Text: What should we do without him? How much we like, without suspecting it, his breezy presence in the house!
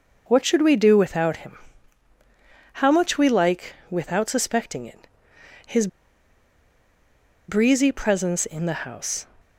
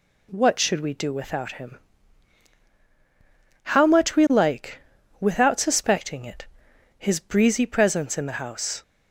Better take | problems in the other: second | pauses between "his" and "breezy"; strong; at 5.8 s; 1.6 s long

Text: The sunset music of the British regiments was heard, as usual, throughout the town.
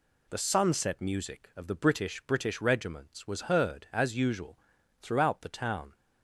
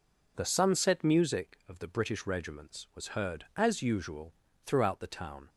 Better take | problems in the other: second | says "British" twice; at 2.2 s

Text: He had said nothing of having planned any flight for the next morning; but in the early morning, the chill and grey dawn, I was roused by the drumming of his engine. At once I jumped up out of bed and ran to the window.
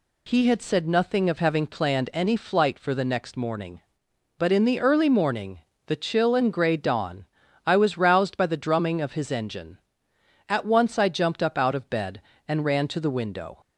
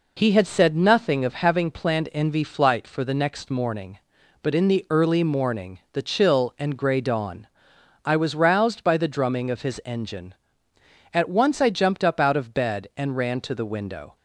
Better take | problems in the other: first | says "envy" for "any"; at 2.1 s

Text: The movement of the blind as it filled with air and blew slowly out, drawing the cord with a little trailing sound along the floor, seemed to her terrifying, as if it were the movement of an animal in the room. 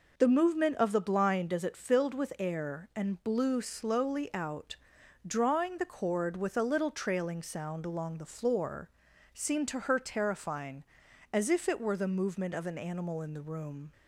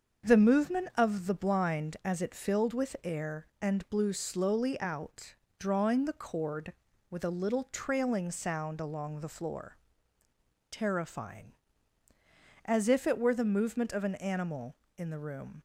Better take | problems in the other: first | starts louder than the rest; until 1.3 s; 7 dB // skips "seemed to her"; at 10.2 s

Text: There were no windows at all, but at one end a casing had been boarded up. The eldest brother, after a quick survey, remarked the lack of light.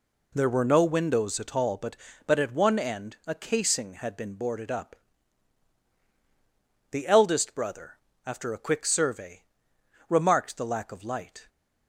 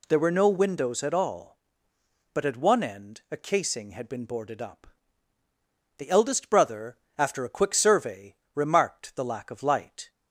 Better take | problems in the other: second | says "but" twice; at 2.2 s

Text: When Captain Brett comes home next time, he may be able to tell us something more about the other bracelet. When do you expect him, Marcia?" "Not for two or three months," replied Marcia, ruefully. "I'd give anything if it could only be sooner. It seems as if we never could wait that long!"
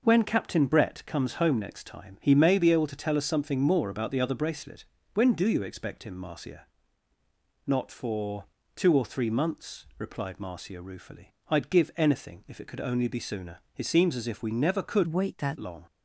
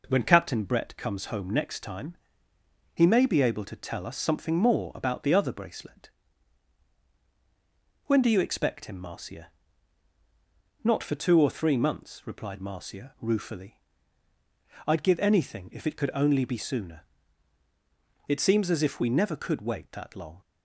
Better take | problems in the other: second | pauses between "for" and "two"; slight; at 8.4 s; 0.32 s long // changes voice from "wait" to "that"; from 15.0 to 15.5 s; 0.5 s long

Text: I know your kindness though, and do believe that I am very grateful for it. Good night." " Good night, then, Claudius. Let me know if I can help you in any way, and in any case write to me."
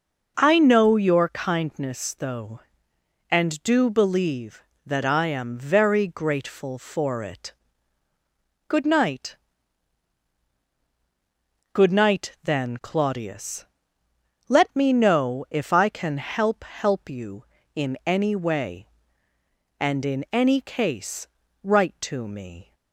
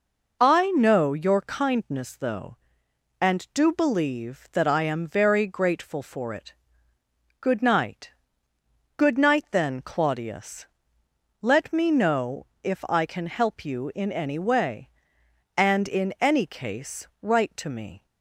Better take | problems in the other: second | starts louder than the rest; strong; until 1.3 s; 7.5 dB // says "help" twice; at 16.6 s // pauses between "case" and "write"; slight; at 21.2 s; 0.36 s long

